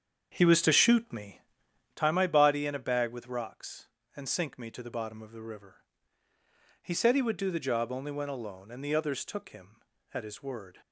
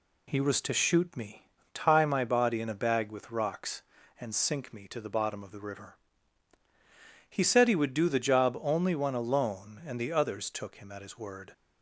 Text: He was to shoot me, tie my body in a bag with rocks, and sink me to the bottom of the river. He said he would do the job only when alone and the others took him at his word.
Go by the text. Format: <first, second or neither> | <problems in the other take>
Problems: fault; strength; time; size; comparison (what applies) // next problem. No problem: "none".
second | starts louder than the rest; strong; until 2.0 s; 7.5 dB